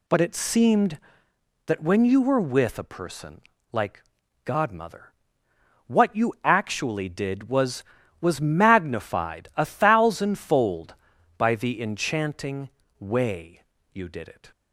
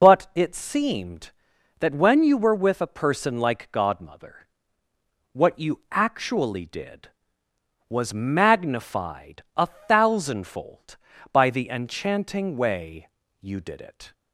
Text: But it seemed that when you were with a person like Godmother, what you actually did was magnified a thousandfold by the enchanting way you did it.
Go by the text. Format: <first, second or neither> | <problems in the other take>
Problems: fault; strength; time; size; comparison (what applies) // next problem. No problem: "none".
second | pauses between "person" and "like"; slight; at 3.4 s; 0.32 s long // pauses between "like" and "Godmother"; at 4.0 s; 0.42 s long // says "was" twice; at 8.2 s // pauses between "enchanting" and "way"; slight; at 12.6 s; 0.30 s long // pauses between "way" and "you"; slight; at 13.6 s; 0.32 s long; slight in the second